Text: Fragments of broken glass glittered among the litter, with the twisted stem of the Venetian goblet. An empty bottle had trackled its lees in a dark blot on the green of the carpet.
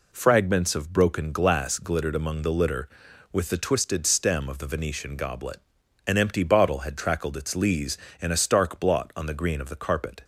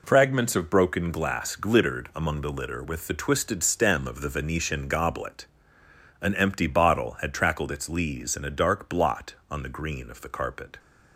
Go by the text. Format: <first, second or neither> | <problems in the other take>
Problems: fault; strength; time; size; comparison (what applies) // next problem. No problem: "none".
second | says "stark" for "dark"; at 8.3 s